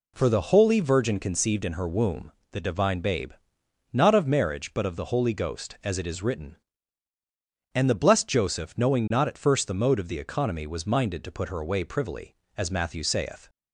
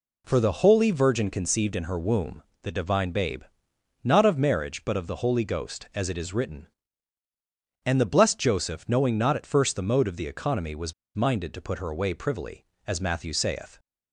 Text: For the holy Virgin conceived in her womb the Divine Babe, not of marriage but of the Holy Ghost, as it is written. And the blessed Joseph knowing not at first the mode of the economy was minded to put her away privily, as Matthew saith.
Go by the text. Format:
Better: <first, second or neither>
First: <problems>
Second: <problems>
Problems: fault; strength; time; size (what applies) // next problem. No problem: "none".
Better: first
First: pauses between "womb" and "the"; slight; at 2.3 s; 0.22 s long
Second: pauses between "womb" and "the"; slight; at 2.4 s; 0.22 s long // pauses between "was" and "minded"; slight; at 10.9 s; 0.23 s long